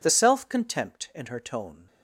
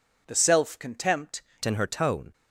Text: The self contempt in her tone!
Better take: first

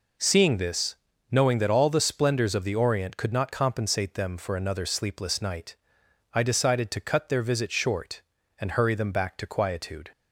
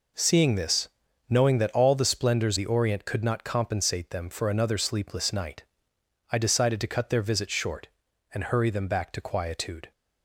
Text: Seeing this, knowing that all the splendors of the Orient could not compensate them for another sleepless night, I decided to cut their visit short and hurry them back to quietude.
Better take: first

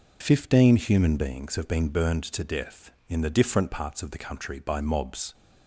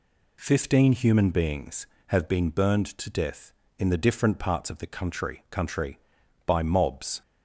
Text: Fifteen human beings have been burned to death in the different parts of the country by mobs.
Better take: first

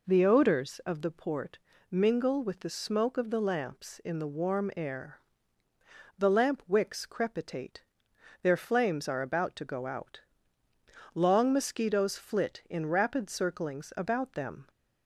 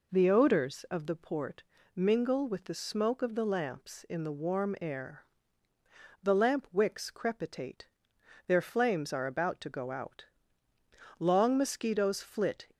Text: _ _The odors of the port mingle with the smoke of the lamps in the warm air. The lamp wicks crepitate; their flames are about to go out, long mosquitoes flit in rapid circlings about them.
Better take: first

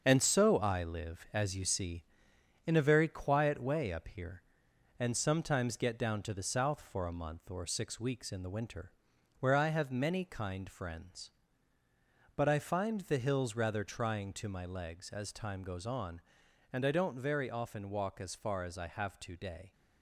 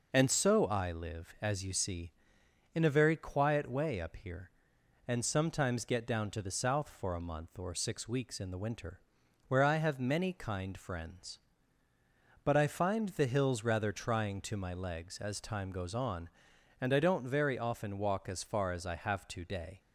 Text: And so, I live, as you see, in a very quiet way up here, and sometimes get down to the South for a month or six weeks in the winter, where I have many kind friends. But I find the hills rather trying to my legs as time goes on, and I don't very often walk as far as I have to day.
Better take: second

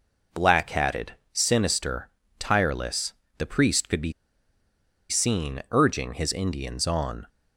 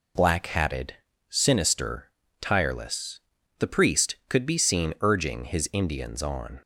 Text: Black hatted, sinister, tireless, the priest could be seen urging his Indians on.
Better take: second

